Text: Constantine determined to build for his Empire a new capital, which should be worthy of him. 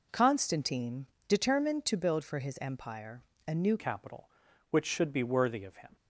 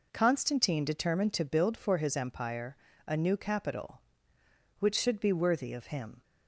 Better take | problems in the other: second | pauses between "Constantine" and "determined"; slight; at 1.0 s; 0.24 s long // pauses between "Empire" and "a"; slight; at 3.2 s; 0.24 s long; slight in the second // changes voice at "capital"; from 3.7 s on; 2.2 s long

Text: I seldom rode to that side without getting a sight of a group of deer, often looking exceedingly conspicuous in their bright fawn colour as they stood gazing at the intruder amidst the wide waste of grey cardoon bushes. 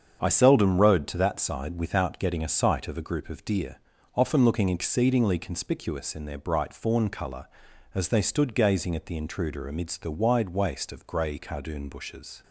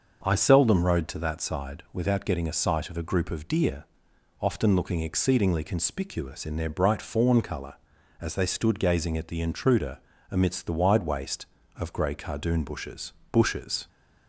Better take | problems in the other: first | starts louder than the rest; until 1.2 s; 6.5 dB; strong in the first // pauses between "intruder" and "amidst"; slight; at 9.9 s; 0.32 s long // says "bushes" twice; at 13.3 s

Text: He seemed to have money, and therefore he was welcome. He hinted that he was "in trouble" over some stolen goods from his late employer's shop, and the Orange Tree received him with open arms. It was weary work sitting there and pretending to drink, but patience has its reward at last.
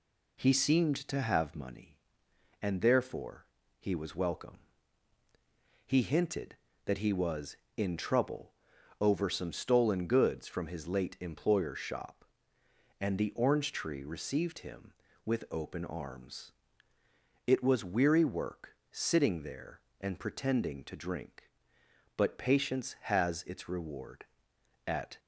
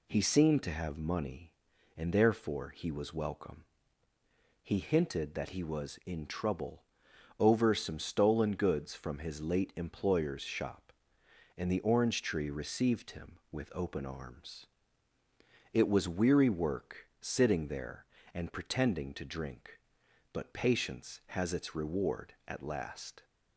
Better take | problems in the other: second | pauses between "therefore" and "he"; slight; at 3.4 s; 0.32 s long // pauses between "trouble" and "over"; noticeable; at 8.5 s; 0.48 s long; noticeable in the second // pauses between "work" and "sitting"; slight; at 18.7 s; 0.16 s long // stops before "last"; at 25.1 s

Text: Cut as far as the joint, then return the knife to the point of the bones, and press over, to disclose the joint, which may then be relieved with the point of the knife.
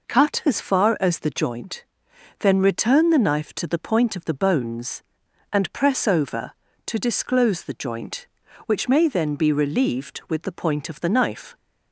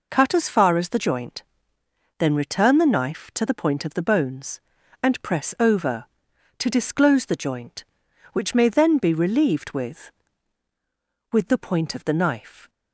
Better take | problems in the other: first | says "with" twice; at 11.3 s

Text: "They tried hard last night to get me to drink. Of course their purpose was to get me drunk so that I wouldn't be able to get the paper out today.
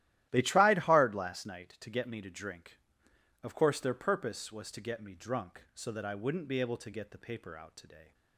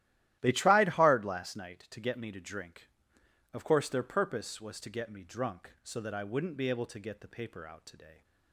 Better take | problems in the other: neither | starts louder than the rest; strong; the same in both

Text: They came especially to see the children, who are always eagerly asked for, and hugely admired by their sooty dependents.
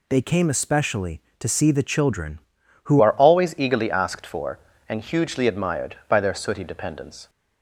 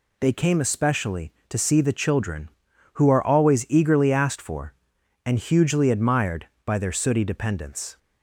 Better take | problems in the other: second | changes voice at "are"; from 3.0 s on; 4.2 s long

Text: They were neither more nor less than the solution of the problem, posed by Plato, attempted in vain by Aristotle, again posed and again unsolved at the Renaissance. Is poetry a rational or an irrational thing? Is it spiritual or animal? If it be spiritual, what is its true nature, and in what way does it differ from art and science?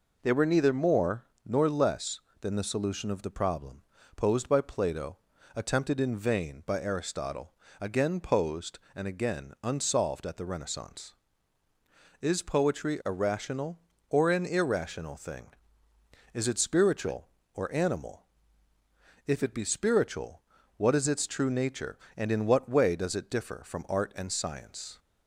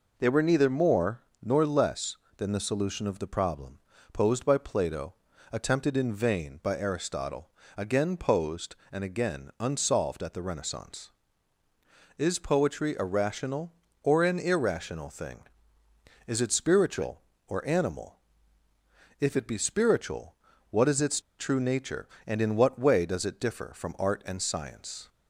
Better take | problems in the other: first | pauses between "more" and "nor"; slight; at 1.2 s; 0.20 s long; slight in the first // pauses between "its" and "true"; slight; at 21.1 s; 0.18 s long

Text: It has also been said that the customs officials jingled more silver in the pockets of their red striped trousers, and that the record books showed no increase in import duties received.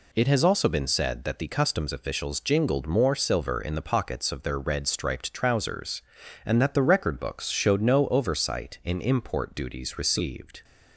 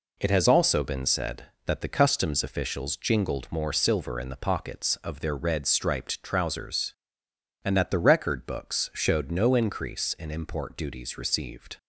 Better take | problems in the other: second | says "oversight" for "increase"; at 8.0 s

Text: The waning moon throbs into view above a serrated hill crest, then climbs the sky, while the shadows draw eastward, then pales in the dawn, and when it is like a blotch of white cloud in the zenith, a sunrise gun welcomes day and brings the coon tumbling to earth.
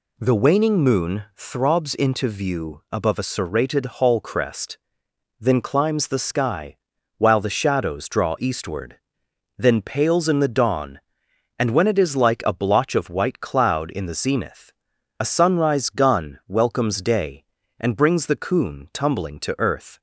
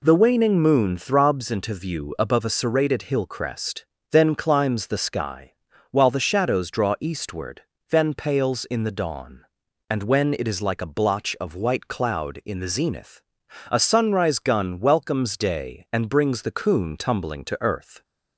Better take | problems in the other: second | says "hall" for "hill"; at 3.8 s

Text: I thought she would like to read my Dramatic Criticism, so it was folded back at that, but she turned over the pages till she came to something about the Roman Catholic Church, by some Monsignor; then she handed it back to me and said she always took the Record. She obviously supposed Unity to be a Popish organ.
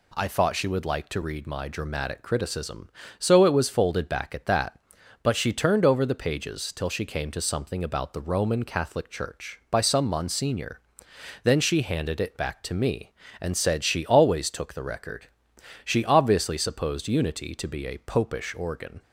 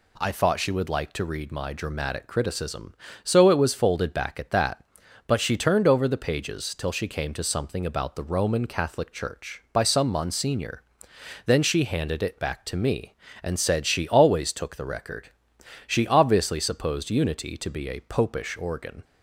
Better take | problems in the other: neither | none

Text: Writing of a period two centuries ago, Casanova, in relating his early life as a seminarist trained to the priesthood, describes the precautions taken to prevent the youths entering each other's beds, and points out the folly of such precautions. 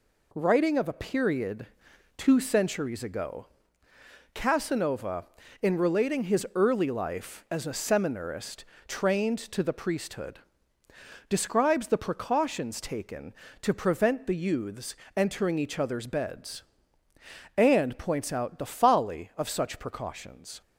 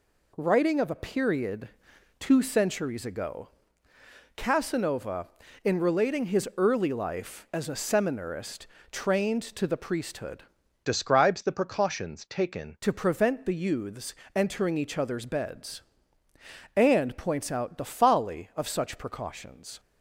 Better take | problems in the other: first | pauses between "period" and "two"; noticeable; at 1.6 s; 0.50 s long; noticeable in the first // pauses between "seminarist" and "trained"; slight; at 8.6 s; 0.24 s long; slight in the first // changes voice from "describes" to "taken"; from 10.8 to 12.7 s; 1.9 s long // pauses between "youths" and "entering"; slight; at 14.1 s; 0.22 s long; slight in the first

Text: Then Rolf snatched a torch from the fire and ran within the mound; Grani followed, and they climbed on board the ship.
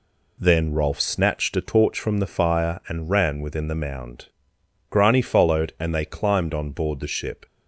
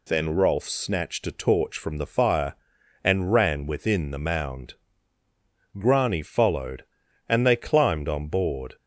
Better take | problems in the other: first | stops before "the ship"; at 8.7 s

